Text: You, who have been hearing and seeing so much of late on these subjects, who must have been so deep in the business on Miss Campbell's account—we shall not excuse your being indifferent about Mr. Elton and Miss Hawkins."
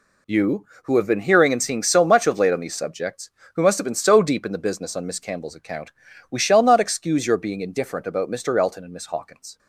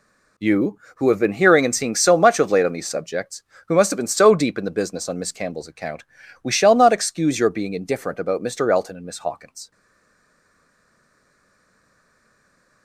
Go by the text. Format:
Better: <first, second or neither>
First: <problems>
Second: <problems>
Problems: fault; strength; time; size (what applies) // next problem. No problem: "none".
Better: first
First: none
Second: stays silent after the last word; strong; from 9.7 s on; 3.1 s long